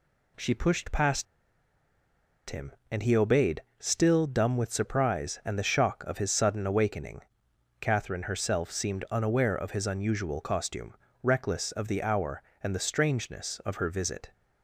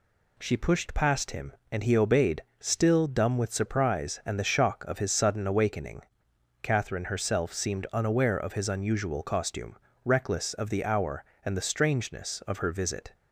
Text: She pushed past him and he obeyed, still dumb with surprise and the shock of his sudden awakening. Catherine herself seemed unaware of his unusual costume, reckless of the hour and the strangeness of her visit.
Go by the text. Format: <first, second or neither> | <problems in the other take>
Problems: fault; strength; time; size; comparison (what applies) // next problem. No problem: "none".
second | pauses between "past" and "him"; strong; at 1.2 s; 1.2 s long